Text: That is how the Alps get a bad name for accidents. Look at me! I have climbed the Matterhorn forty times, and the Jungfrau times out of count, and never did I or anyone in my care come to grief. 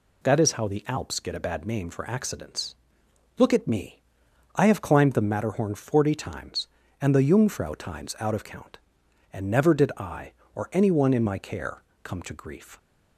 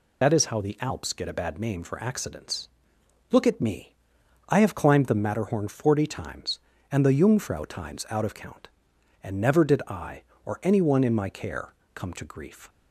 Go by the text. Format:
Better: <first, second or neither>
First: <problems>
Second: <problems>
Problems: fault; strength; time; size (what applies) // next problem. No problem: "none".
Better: first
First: pauses between "care" and "come"; slight; at 11.8 s; 0.22 s long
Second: loses the start of "That"; at 0.2 s; 55 ms // pauses between "care" and "come"; slight; at 11.7 s; 0.22 s long